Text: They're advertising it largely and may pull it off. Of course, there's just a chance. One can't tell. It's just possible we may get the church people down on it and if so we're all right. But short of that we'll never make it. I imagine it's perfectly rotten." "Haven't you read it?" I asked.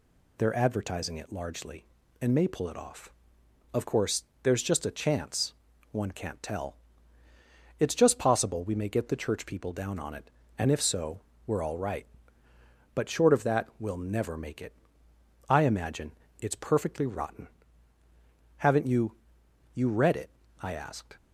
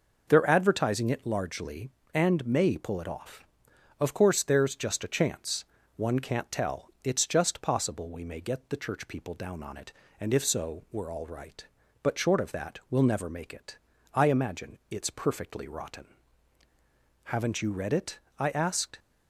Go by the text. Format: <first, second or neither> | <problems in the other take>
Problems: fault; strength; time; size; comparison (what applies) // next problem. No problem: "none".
second | pauses between "so" and "we're"; slight; at 11.2 s; 0.26 s long // pauses between "imagine" and "it's"; slight; at 16.1 s; 0.30 s long // says "you" twice; at 19.7 s